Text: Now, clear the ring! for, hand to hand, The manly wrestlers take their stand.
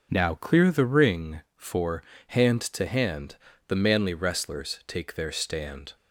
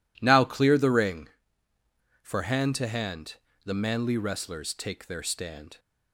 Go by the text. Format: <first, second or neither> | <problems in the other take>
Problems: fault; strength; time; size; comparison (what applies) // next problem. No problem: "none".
neither | none